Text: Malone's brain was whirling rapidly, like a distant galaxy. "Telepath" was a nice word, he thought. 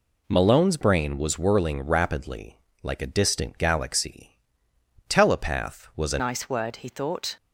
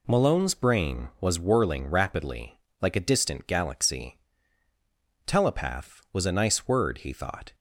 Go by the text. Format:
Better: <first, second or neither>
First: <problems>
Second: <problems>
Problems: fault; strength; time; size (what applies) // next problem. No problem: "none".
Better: second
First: changes voice at "nice"; from 6.2 s on; 1.1 s long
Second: none